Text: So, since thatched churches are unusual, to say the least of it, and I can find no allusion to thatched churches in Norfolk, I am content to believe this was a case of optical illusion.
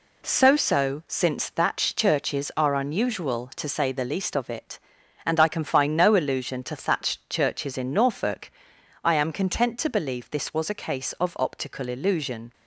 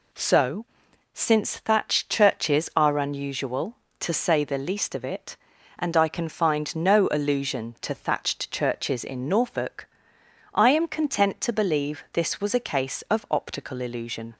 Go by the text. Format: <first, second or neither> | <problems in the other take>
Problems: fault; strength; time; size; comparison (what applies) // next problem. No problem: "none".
second | says "So" twice; at 0.5 s